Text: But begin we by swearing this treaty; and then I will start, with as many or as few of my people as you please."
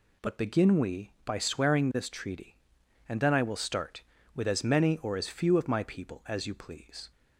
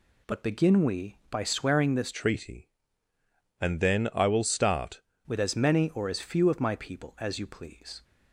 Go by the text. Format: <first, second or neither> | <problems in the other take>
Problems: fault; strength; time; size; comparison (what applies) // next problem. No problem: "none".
first | changes voice from "treaty" to "start"; from 2.1 to 5.0 s; 2.9 s long